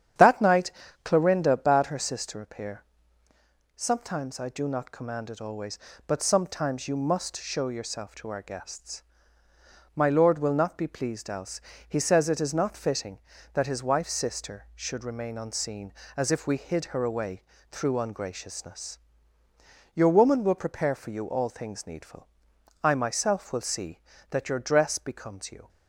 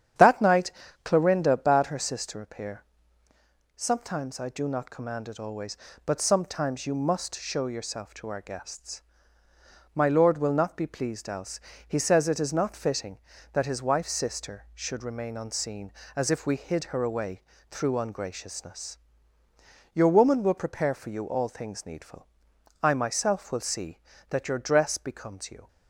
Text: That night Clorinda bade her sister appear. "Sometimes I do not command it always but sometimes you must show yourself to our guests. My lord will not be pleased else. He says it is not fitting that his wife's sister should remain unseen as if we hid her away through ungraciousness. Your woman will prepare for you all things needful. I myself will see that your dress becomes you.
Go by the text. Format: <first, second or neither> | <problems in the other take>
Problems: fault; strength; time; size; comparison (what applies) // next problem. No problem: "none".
neither | starts louder than the rest; strong; the same in both // pauses between "night" and "Clorinda"; slight; the same in both // pauses between "away" and "through"; slight; the same in both